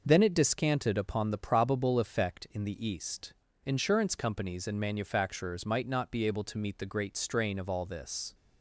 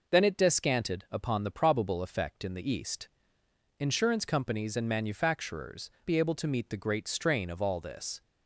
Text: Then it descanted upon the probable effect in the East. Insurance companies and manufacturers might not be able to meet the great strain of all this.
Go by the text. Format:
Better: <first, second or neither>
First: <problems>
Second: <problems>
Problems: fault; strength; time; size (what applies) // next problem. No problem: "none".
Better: first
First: none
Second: skips "might not"; at 5.9 s